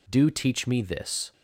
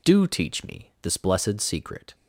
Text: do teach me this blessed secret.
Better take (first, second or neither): second